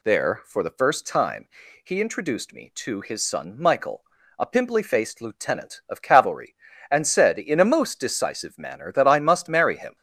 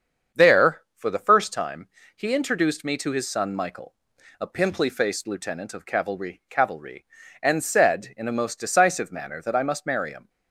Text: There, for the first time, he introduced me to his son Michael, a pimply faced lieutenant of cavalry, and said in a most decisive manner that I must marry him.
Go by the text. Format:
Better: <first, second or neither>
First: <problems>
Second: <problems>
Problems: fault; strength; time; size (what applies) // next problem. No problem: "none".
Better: first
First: none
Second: starts louder than the rest; strong; until 1.4 s; 7 dB // says "cavalry" twice; at 6.4 s